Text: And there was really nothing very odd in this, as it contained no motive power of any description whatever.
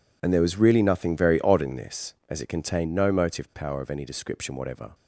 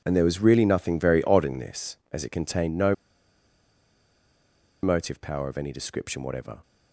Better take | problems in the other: first | pauses between "no" and "motive"; strong; at 2.9 s; 1.8 s long

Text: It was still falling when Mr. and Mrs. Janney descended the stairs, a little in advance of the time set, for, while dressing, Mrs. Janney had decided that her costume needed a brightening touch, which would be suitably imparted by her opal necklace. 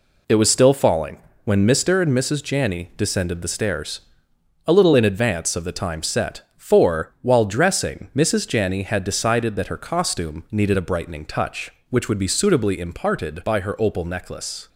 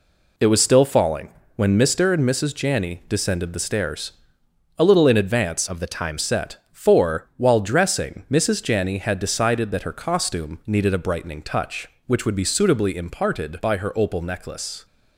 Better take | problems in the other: first | pauses between "falling" and "when"; slight; at 1.3 s; 0.24 s long; slight in the first // changes voice from "of" to "time"; from 5.6 to 6.1 s; 0.5 s long

